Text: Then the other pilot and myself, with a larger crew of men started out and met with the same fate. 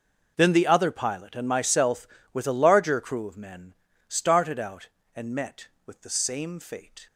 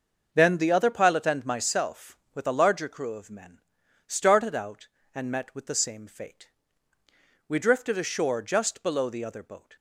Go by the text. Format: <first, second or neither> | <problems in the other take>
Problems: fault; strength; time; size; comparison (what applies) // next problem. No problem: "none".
first | starts louder than the rest; until 1.3 s; 6.5 dB // pauses between "men" and "started"; noticeable; at 3.5 s; 0.46 s long; slight in the first // goes on to say "We drifted ashore just below the other boat"; strong; from 7.4 s on; 2.2 s long